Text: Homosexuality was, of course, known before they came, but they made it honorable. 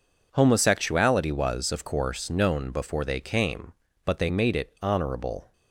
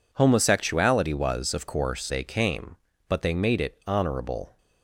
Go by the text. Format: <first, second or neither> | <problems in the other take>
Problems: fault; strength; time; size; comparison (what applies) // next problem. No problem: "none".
first | skips "known before"; at 2.1 s